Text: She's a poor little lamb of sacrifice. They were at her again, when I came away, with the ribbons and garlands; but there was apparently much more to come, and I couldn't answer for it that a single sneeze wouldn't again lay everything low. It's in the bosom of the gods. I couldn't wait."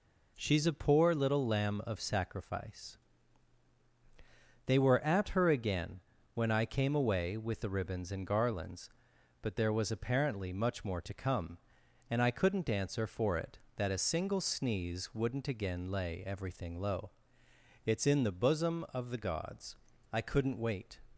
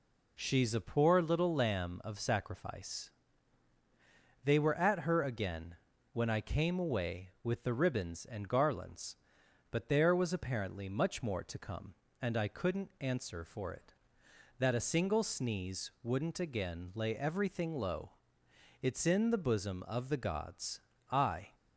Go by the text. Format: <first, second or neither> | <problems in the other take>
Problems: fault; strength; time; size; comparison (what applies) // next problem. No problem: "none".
first | stops before "couldn't wait"; at 21.5 s